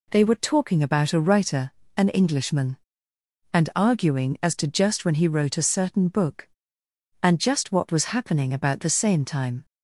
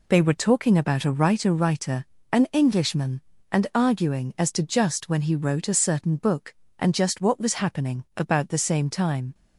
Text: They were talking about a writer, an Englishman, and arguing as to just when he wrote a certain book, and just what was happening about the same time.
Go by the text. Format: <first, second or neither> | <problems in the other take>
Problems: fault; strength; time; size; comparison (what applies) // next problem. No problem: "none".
first | says "writer" twice; at 1.5 s